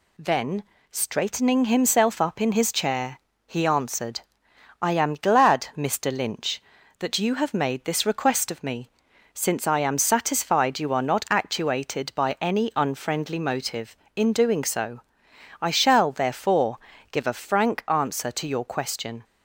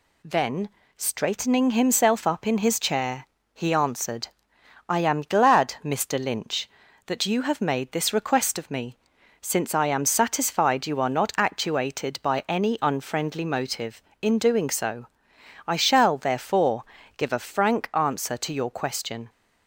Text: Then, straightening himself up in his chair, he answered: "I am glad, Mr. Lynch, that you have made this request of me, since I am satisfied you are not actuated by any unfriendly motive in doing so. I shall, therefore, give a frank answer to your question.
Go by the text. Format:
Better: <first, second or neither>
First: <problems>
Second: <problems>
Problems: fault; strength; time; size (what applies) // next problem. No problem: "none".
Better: neither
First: none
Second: none